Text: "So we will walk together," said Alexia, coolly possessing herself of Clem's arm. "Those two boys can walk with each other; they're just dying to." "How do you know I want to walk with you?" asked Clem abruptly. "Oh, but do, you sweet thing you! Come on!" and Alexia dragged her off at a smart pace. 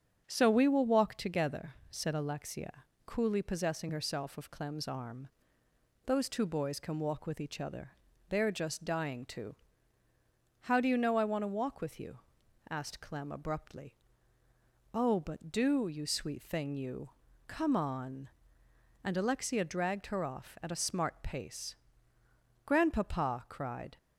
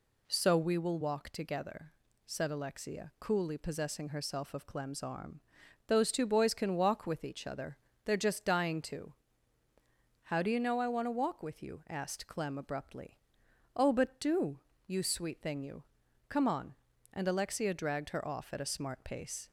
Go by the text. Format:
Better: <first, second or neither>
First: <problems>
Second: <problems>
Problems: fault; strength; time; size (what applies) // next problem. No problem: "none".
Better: second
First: starts louder than the rest; strong; until 1.2 s; 7 dB // goes on to say "Grandpapa cried"; from 22.6 s on; 1.3 s long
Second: none